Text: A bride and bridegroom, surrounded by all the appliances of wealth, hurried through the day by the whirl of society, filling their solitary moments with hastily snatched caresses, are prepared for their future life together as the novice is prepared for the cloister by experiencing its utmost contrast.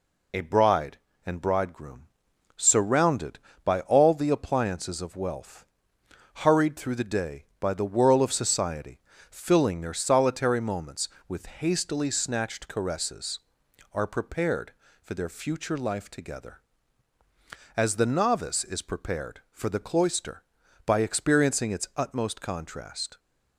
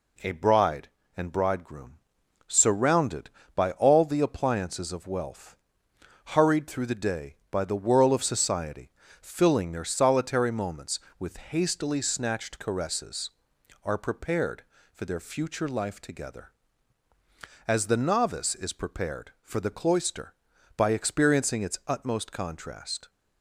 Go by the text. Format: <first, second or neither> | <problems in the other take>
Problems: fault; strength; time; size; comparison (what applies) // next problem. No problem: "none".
second | loses the start of "A"; at 0.3 s; 65 ms